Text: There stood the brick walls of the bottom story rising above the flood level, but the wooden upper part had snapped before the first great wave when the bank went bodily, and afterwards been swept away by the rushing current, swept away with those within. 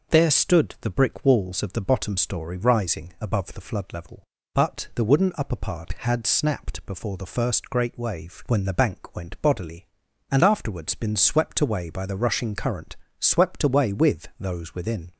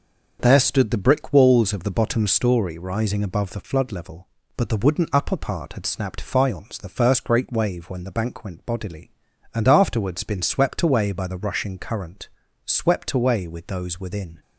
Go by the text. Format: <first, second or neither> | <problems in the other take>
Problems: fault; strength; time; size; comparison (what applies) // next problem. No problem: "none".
first | starts louder than the rest; until 1.4 s; 6.5 dB // says "faience" for "before"; at 6.2 s